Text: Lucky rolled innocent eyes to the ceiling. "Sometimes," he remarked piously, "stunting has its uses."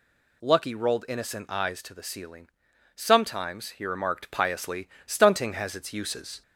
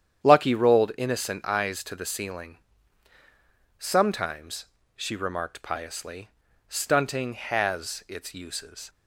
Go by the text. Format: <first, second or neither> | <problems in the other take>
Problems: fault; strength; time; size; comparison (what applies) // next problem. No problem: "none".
first | starts louder than the rest; strong; until 1.3 s; 9 dB // says "she" for "he"; at 4.9 s